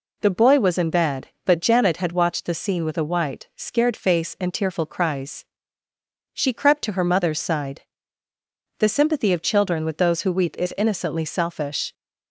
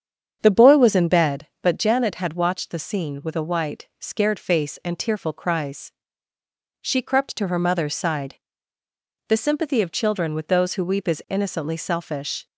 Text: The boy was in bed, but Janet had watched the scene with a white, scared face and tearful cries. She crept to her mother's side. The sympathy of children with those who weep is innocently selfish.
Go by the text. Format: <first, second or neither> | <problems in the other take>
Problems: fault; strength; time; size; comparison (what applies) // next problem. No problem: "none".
first | starts louder than the rest; strong; until 1.4 s; 8 dB